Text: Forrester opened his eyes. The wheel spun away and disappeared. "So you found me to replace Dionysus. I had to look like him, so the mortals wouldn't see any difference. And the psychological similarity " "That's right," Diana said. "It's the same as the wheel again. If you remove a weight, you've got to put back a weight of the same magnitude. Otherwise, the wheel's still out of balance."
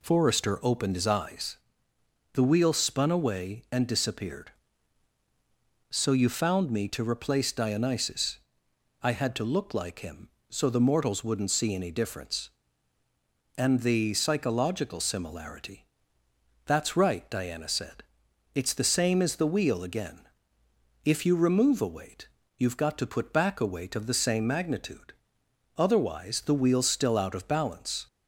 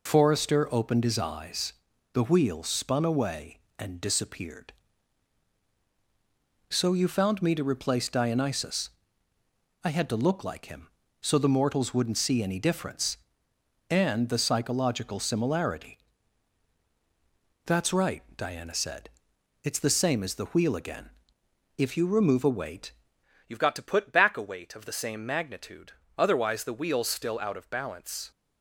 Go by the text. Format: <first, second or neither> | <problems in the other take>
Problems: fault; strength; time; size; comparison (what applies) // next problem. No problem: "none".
first | changes voice at "you've"; from 23.4 s on; 4.9 s long